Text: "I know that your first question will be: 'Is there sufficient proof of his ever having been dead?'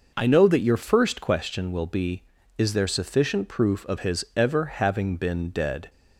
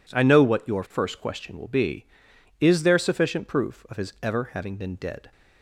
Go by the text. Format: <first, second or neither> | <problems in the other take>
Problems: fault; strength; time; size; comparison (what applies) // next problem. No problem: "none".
first | says "what" for "that"; at 0.4 s